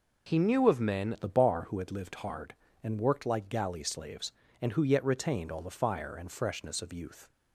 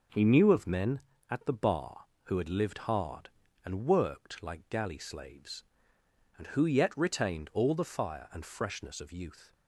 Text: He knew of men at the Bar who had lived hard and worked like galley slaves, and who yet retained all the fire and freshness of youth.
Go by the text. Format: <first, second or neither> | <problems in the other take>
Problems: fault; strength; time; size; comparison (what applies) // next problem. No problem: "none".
second | changes voice at "at"; from 1.1 s on; 6.1 s long